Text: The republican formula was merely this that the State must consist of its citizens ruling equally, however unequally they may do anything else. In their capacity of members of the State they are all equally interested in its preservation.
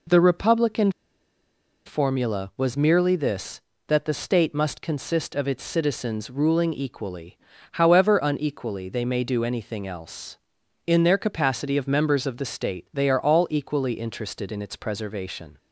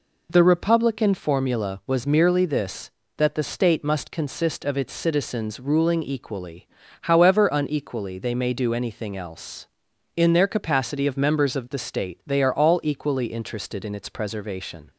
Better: second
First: pauses between "republican" and "formula"; noticeable; at 0.9 s; 0.93 s long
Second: none

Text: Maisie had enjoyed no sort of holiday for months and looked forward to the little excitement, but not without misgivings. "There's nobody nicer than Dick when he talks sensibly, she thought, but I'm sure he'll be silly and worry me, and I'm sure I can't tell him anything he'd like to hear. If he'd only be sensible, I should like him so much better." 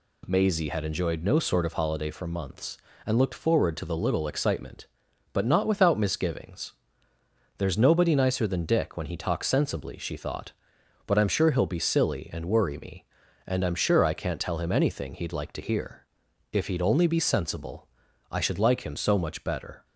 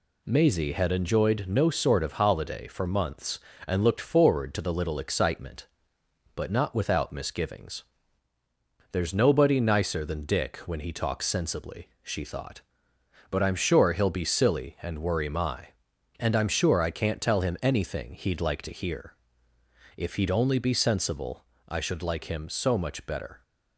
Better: first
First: none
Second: says "my" for "me"; at 15.2 s

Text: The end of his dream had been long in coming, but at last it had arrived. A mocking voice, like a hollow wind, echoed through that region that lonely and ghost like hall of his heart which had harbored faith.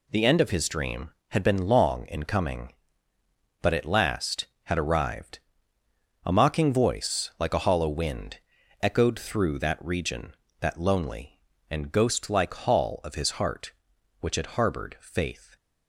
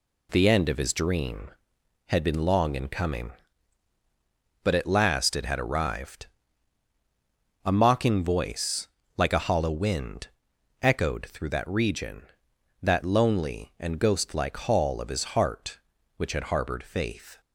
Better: second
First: skips "it"; at 4.5 s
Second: none

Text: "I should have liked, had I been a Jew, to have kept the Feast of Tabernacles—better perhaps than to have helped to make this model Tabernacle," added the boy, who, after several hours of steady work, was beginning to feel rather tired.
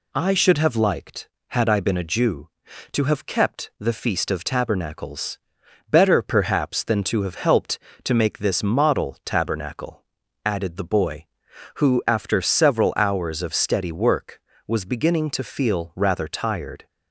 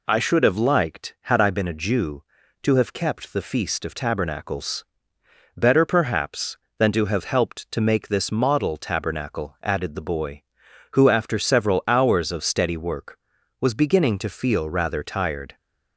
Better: neither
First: none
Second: none

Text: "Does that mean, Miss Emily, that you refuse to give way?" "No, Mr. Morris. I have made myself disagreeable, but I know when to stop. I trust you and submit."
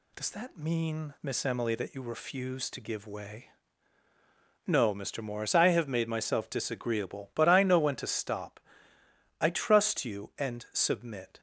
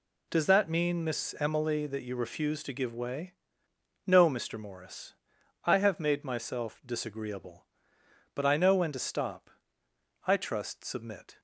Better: first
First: none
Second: skips "you and"; at 10.8 s

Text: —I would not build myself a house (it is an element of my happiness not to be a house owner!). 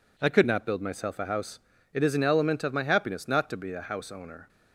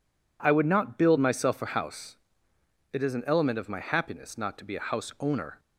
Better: second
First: says "could" for "would"; at 0.3 s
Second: none

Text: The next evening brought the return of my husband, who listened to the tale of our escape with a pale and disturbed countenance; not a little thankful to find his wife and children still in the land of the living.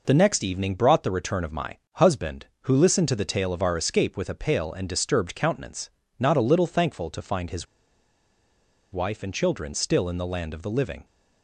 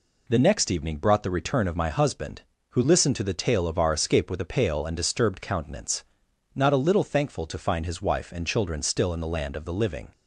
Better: second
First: pauses between "my" and "husband"; slight; at 1.7 s; 0.16 s long // pauses between "his" and "wife"; strong; at 7.6 s; 1.2 s long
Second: none

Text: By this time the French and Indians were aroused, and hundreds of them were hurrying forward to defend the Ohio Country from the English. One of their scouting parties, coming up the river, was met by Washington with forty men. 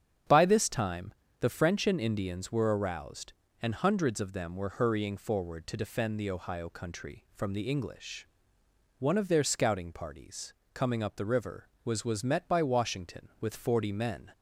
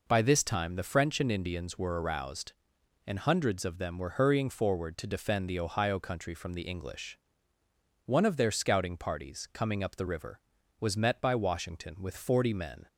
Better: second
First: starts louder than the rest; strong; until 1.5 s; 8 dB // pauses between "time" and "the"; slight; at 1.1 s; 0.26 s long // says "was" twice; at 12.0 s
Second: none

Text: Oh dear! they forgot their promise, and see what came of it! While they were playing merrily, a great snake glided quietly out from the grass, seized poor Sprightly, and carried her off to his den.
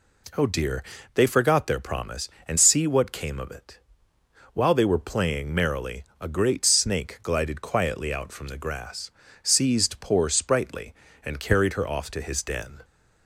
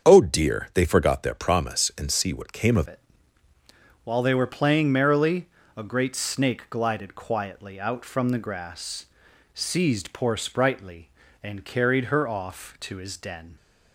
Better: first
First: none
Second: starts louder than the rest; strong; until 1.1 s; 7.5 dB // changes voice at "it"; from 2.8 s on; 10.7 s long

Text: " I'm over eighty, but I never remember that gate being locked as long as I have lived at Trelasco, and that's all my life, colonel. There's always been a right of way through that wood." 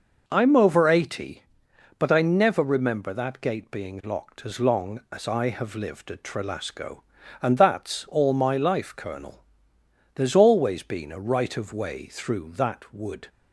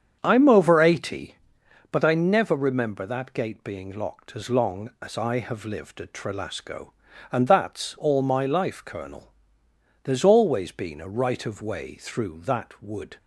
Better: first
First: none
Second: starts louder than the rest; strong; until 1.9 s; 8 dB

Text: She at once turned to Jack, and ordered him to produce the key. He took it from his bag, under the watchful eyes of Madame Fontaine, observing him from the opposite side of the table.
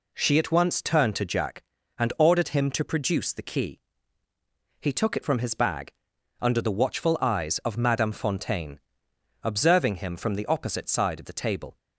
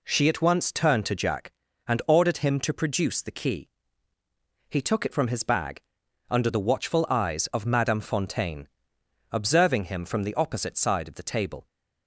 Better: neither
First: none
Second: none

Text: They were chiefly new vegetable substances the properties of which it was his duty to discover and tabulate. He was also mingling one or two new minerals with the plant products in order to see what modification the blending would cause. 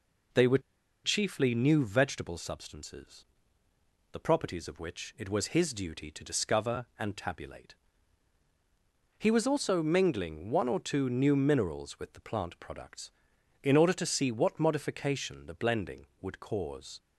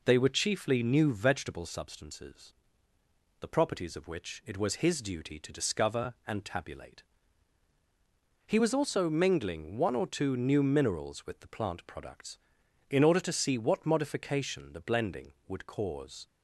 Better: second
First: pauses between "were" and "chiefly"; at 0.5 s; 0.45 s long // pauses between "substances" and "the"; noticeable; at 3.2 s; 0.86 s long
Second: pauses between "substances" and "the"; noticeable; at 2.5 s; 0.86 s long

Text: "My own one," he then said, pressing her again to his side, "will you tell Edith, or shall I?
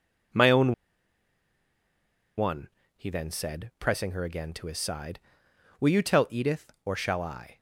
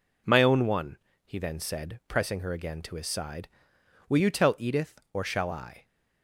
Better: second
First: pauses between "own" and "one"; strong; at 0.7 s; 1.6 s long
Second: none

